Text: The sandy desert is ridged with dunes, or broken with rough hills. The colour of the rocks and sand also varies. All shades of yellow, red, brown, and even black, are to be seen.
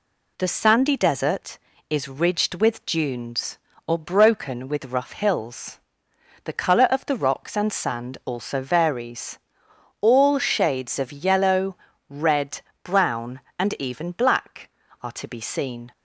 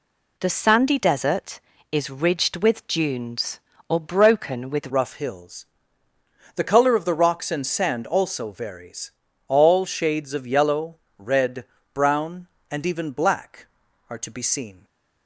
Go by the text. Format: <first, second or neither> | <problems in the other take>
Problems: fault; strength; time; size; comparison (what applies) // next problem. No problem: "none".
first | changes voice at "rough"; from 4.8 s on; 10.0 s long